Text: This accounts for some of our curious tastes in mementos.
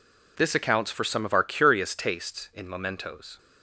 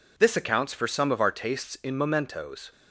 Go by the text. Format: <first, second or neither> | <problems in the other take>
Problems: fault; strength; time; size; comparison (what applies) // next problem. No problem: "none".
first | skips "curious"; at 1.3 s